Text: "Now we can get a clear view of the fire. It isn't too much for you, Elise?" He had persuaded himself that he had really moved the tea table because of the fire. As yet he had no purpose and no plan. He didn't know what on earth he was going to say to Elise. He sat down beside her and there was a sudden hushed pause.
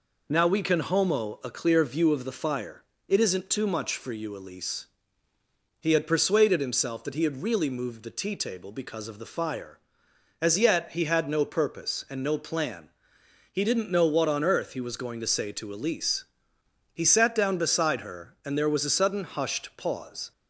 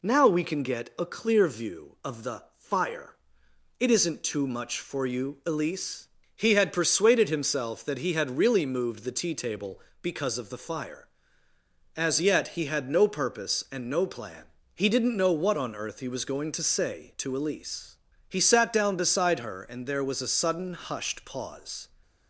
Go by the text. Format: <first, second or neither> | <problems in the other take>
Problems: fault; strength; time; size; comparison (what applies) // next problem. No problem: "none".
second | says "homo" for "get"; at 0.7 s